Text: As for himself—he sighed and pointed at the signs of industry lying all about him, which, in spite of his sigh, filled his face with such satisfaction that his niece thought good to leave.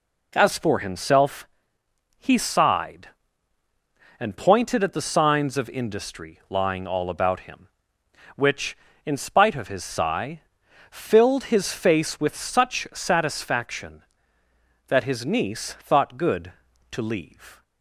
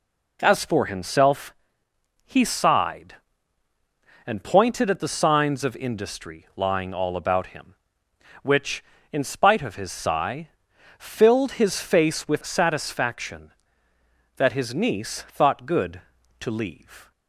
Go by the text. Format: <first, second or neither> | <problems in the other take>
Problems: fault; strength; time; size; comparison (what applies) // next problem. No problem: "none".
first | skips "such"; at 12.4 s